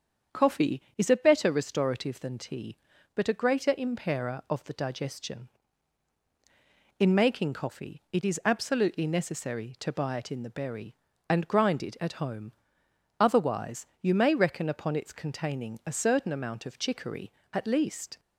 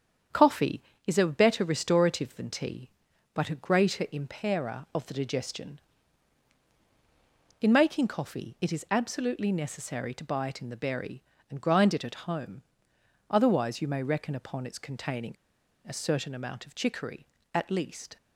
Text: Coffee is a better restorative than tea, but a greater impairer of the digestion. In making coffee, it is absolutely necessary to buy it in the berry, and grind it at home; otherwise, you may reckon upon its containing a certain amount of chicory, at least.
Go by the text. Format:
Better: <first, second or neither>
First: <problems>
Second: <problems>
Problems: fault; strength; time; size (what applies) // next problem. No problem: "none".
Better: first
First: starts louder than the rest; strong; until 1.4 s; 7.5 dB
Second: starts louder than the rest; strong; until 1.5 s; 8 dB // pauses between "containing" and "a"; noticeable; at 15.3 s; 0.51 s long